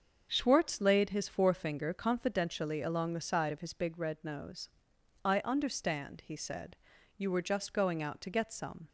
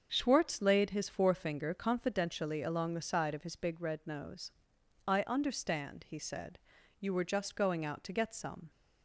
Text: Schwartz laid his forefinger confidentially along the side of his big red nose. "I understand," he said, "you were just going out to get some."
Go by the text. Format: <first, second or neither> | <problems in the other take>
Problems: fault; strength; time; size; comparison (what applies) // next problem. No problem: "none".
neither | starts louder than the rest; the same in both